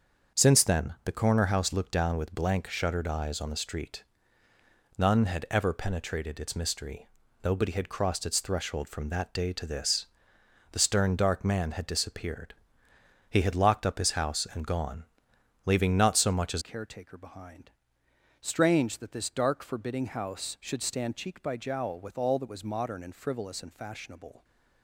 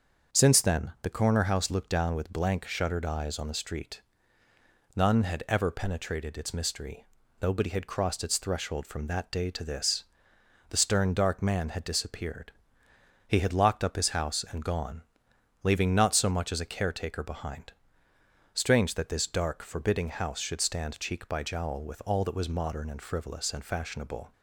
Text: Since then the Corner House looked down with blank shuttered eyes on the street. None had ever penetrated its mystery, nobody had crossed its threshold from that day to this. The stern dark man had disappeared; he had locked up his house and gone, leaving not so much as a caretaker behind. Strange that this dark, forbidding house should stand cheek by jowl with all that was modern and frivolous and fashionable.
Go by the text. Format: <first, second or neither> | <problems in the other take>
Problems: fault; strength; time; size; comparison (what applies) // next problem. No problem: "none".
second | starts louder than the rest; until 1.4 s; 7 dB; also in the second // changes voice at "a"; from 16.6 s on; 7.8 s long